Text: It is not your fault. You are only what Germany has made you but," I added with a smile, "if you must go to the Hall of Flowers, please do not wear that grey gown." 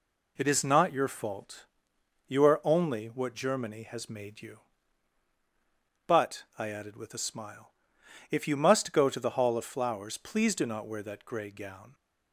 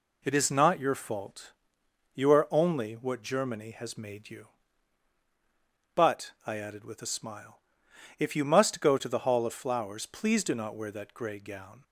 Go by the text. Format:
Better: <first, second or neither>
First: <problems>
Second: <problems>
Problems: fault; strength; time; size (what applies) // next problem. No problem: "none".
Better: neither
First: none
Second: none